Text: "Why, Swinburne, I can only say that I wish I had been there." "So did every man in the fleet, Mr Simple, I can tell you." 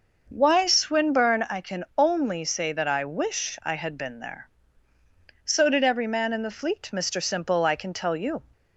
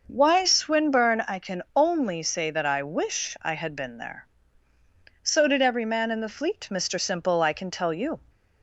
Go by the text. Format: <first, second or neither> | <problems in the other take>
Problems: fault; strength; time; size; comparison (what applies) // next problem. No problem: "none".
neither | none